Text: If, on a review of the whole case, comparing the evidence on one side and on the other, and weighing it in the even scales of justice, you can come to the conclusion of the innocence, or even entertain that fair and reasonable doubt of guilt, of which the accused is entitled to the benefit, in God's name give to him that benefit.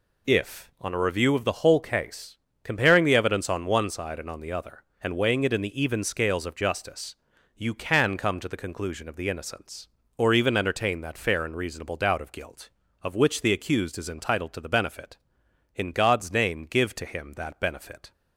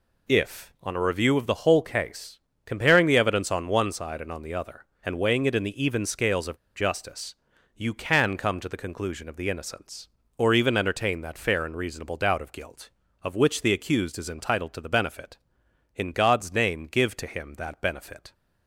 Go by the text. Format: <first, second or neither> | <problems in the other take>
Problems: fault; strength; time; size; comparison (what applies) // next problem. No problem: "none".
first | pauses between "of" and "justice"; slight; at 6.5 s; 0.18 s long